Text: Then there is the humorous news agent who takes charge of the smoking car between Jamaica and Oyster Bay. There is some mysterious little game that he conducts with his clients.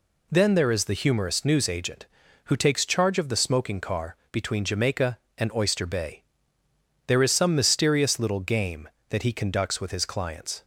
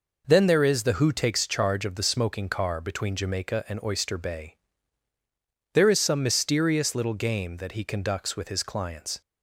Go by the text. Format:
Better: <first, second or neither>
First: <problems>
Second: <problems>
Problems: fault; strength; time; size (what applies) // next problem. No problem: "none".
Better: first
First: none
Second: skips "humorous news agent"; at 0.9 s